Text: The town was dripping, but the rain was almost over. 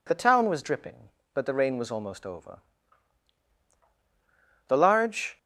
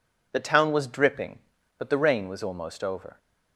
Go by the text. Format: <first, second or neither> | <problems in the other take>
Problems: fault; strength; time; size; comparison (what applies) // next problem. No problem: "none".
second | goes on to say "The large"; noticeable; from 4.6 s on; 0.70 s long